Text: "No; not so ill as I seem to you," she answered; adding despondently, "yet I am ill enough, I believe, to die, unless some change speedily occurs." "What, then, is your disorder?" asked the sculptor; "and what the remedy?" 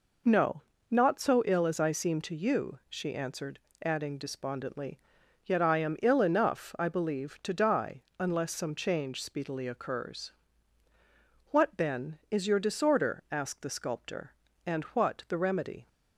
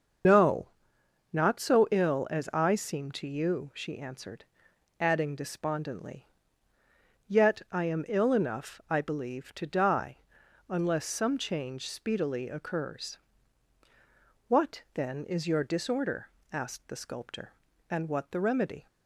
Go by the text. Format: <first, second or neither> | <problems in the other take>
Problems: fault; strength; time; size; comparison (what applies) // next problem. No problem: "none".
first | loses the start of "No"; at 0.2 s; 85 ms // starts louder than the rest; until 1.8 s; 6.5 dB